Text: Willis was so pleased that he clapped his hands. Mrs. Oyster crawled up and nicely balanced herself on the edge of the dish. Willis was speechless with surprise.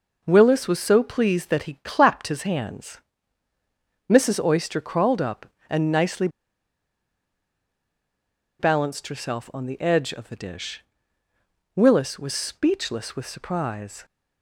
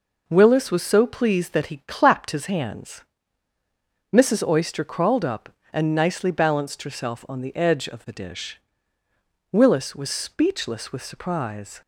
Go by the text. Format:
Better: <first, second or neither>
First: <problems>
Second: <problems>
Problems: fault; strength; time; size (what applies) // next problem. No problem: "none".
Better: second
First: pauses between "nicely" and "balanced"; strong; at 6.2 s; 2.3 s long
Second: none